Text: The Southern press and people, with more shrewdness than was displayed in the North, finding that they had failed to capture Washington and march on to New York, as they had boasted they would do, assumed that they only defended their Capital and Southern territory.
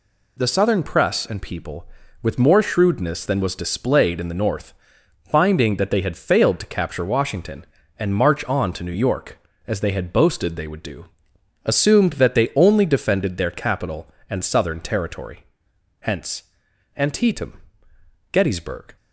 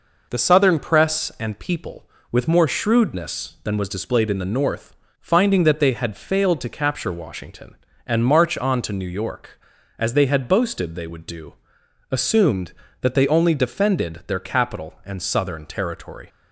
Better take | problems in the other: second | goes on to say "Hence Antietam Gettysburg"; strong; from 15.9 s on; 2.9 s long

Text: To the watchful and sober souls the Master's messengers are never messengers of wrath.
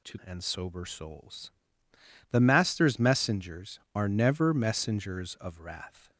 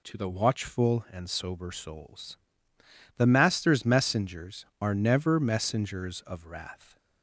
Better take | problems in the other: second | skips "the watchful"; at 0.2 s // pauses between "souls" and "the"; noticeable; at 1.5 s; 0.80 s long; noticeable in the second

